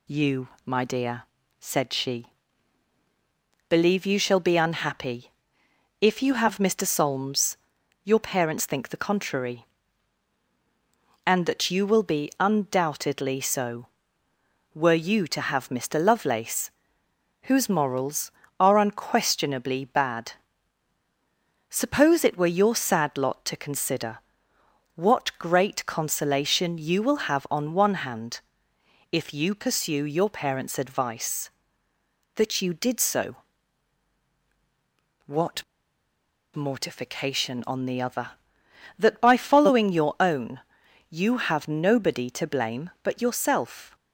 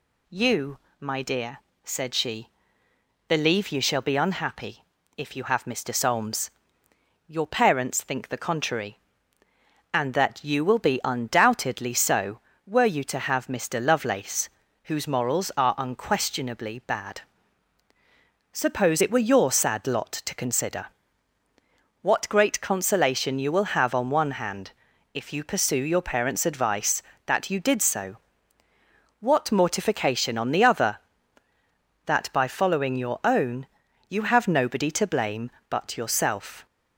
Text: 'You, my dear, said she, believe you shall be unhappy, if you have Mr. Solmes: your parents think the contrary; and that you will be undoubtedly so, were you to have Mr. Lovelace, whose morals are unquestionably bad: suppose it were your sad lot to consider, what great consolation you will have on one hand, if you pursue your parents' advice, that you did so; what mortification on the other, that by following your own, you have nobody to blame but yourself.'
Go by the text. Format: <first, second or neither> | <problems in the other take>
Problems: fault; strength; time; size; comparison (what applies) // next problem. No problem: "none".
second | pauses between "what" and "mortification"; noticeable; at 35.6 s; 0.91 s long